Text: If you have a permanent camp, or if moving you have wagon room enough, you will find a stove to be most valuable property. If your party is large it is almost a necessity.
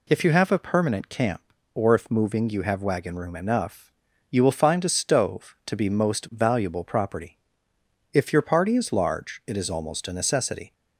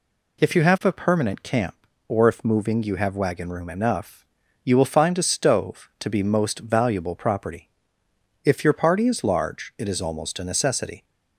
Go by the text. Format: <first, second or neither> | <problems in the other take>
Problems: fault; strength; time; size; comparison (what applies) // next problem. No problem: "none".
neither | none